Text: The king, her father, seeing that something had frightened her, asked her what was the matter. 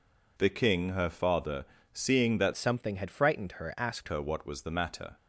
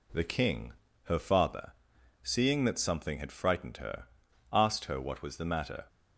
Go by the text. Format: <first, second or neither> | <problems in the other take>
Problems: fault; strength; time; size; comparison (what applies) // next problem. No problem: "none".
second | changes voice from "something" to "asked"; from 2.5 to 4.0 s; 1.5 s long